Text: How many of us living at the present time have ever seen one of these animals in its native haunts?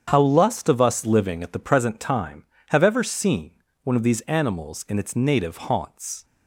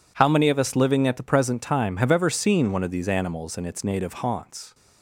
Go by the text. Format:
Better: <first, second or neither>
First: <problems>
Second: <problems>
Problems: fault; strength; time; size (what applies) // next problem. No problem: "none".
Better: second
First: starts louder than the rest; strong; until 1.0 s; 8 dB // says "lust" for "many"; at 0.2 s // pauses between "seen" and "one"; slight; at 3.5 s; 0.32 s long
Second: none